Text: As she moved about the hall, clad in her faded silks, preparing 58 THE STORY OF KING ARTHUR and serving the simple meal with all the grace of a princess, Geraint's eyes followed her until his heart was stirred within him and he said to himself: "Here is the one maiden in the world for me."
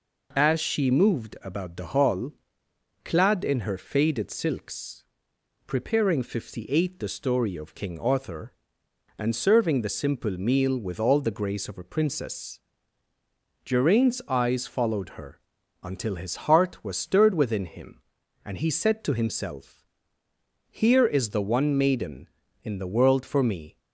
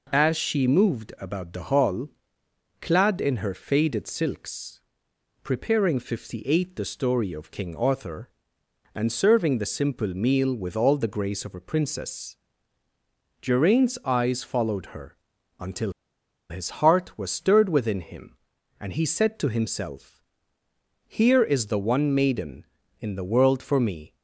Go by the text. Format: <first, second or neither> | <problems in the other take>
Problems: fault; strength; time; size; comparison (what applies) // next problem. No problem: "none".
first | pauses between "her" and "until"; at 15.1 s; 0.42 s long; also in the first // pauses between "until" and "his"; noticeable; at 15.9 s; 0.57 s long